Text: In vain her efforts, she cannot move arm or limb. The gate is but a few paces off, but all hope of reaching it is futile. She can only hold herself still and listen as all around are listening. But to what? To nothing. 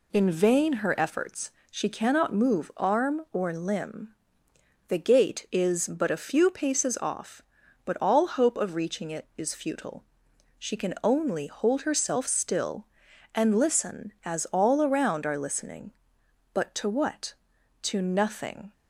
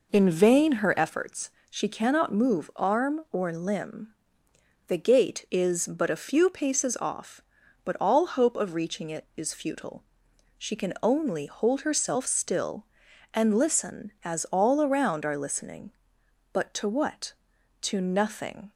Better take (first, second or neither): first